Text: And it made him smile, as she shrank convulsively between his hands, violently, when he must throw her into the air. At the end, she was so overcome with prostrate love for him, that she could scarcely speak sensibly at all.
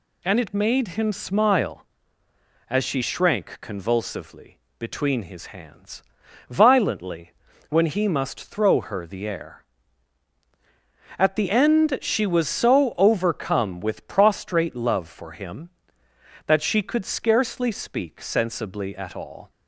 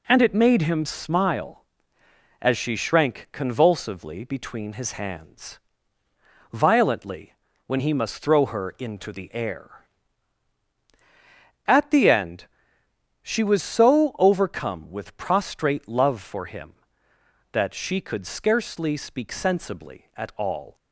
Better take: second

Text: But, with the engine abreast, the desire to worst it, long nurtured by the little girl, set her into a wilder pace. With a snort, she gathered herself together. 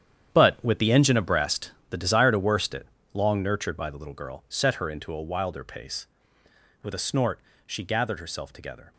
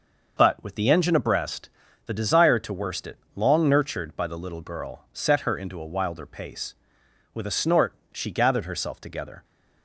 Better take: second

